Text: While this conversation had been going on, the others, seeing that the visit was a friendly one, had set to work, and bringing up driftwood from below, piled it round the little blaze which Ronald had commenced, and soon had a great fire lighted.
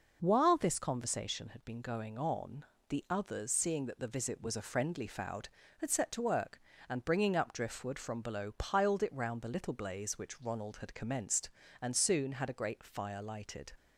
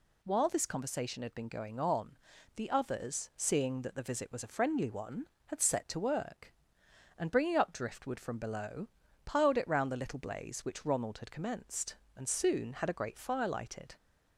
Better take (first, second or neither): second